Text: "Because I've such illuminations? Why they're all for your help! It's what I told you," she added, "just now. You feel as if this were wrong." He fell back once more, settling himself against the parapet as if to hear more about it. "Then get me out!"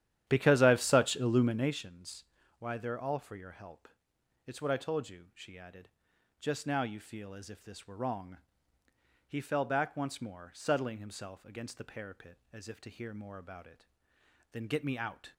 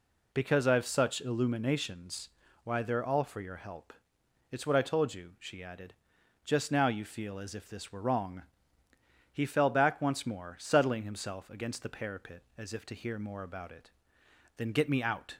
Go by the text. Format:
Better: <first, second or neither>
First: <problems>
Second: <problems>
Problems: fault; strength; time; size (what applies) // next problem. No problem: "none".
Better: second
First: starts louder than the rest; strong; until 1.8 s; 11.5 dB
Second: none